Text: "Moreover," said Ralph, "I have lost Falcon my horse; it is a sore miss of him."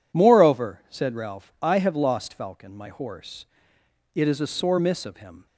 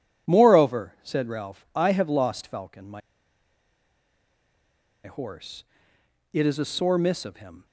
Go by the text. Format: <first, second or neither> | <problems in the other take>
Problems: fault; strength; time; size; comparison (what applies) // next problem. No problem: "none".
first | pauses between "my" and "horse"; strong; at 3.0 s; 2.0 s long